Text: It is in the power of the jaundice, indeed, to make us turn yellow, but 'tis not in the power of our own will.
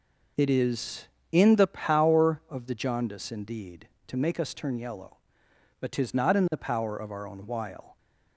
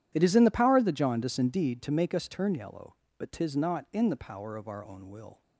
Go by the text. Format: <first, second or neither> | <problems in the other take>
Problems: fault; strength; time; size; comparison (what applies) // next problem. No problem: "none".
second | says "while" for "will"; at 7.4 s